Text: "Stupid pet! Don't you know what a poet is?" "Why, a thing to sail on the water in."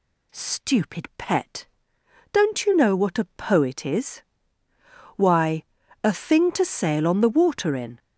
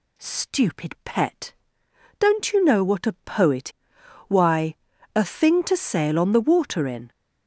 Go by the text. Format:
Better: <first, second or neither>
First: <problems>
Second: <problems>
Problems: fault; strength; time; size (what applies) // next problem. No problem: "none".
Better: first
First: none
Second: skips "is"; at 3.9 s